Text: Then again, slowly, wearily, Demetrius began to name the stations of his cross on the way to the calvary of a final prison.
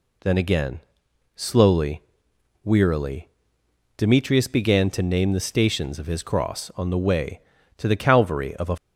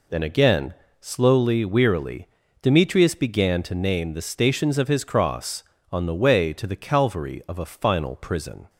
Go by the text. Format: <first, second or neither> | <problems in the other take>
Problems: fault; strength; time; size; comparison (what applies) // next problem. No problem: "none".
second | stops before "final prison"; at 8.7 s